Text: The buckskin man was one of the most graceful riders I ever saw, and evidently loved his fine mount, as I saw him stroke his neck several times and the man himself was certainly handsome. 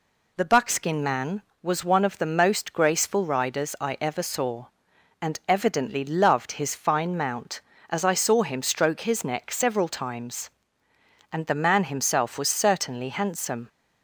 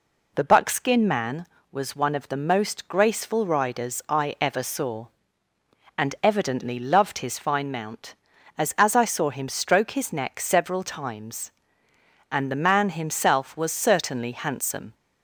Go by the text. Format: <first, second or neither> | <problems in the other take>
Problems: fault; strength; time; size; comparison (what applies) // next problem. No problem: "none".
first | says "as" twice; at 8.7 s